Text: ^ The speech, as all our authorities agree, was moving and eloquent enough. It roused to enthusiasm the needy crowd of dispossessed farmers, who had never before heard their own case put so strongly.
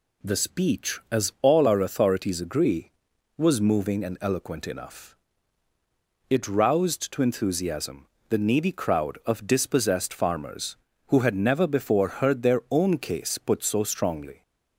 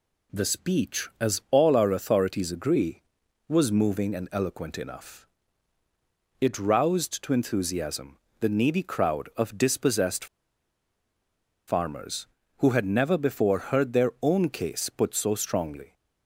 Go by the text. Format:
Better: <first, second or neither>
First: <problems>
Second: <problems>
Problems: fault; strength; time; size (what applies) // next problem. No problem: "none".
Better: first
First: pauses between "enthusiasm" and "the"; slight; at 8.0 s; 0.22 s long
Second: pauses between "enthusiasm" and "the"; slight; at 8.1 s; 0.22 s long // pauses between "dispossessed" and "farmers"; strong; at 10.2 s; 1.4 s long